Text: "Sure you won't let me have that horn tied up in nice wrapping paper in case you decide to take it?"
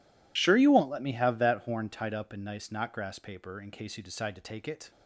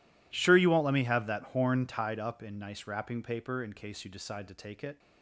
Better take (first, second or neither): second